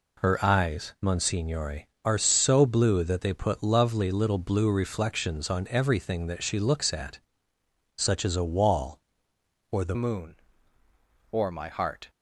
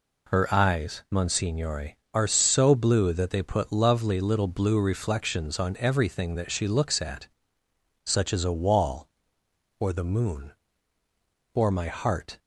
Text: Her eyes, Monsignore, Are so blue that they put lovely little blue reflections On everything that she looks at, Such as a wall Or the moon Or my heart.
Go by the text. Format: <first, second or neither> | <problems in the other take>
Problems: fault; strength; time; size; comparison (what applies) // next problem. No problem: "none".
second | changes voice at "moon"; from 9.9 s on; 2.1 s long